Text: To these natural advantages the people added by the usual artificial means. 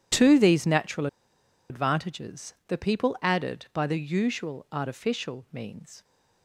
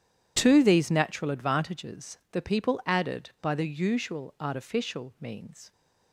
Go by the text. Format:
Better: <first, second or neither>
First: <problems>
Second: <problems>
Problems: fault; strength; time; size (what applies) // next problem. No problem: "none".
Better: second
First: pauses between "natural" and "advantages"; noticeable; at 1.0 s; 0.62 s long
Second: none